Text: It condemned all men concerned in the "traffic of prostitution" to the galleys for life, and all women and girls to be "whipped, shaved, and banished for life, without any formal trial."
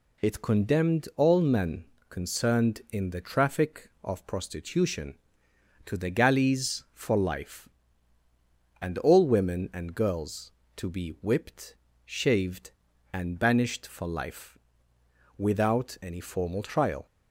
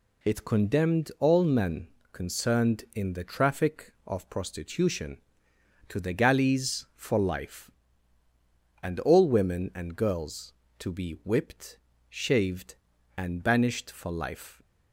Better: first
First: pauses between "men" and "concerned"; slight; at 1.8 s; 0.26 s long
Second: pauses between "men" and "concerned"; slight; at 1.8 s; 0.26 s long // stops before "without any formal trial"; at 14.6 s

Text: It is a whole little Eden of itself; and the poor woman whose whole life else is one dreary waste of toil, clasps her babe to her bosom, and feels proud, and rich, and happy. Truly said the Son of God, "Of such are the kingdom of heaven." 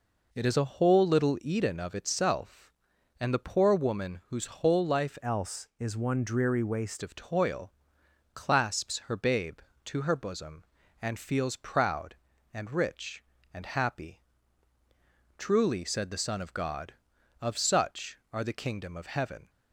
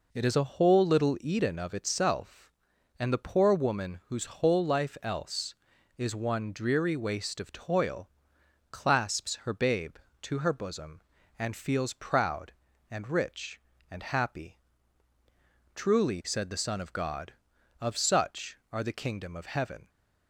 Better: second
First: changes voice from "else" to "waste"; from 5.2 to 7.0 s; 1.8 s long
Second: none

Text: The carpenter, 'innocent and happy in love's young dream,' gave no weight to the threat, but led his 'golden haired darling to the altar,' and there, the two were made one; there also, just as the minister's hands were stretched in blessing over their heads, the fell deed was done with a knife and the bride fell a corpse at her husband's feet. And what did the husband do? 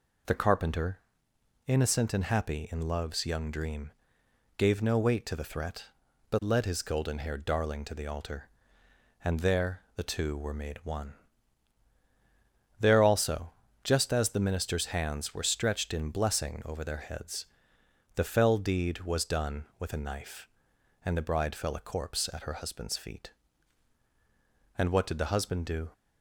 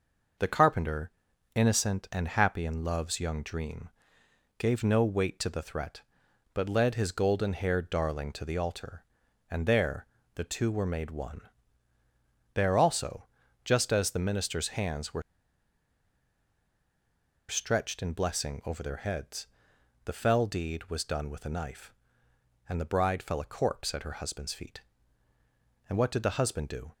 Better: first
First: none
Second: pauses between "were" and "stretched"; strong; at 15.2 s; 2.2 s long

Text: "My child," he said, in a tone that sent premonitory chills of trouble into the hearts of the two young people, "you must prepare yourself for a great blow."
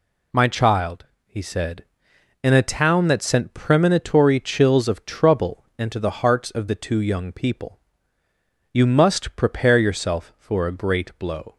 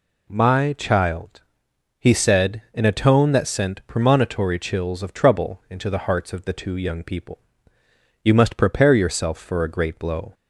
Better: second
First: says "town" for "tone"; at 2.6 s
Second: none

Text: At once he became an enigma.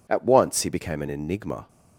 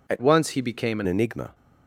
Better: first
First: none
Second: changes voice from "once" to "an"; from 0.2 to 1.0 s; 0.8 s long

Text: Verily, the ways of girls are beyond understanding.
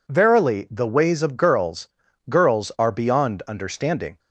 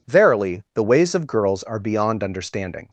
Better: second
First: says "girls" twice; at 2.2 s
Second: none

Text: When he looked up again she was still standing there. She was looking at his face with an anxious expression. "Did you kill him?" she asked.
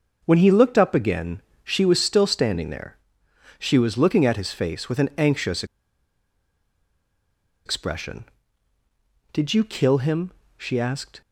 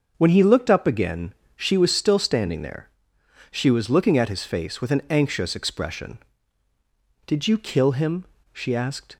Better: second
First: starts louder than the rest; until 1.2 s; 6.5 dB // pauses between "again" and "she"; slight; at 1.4 s; 0.22 s long // pauses between "anxious" and "expression"; strong; at 5.6 s; 2.0 s long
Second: starts louder than the rest; until 1.1 s; 6.5 dB // pauses between "again" and "she"; slight; at 1.3 s; 0.22 s long

